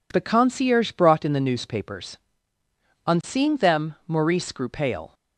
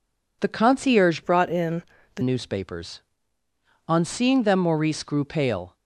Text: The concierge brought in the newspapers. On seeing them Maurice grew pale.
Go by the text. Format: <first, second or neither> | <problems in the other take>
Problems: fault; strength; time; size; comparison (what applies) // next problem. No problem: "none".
first | changes voice from "brought" to "the"; from 1.2 to 2.2 s; 1.0 s long // pauses between "in" and "the"; slight; at 1.8 s; 0.34 s long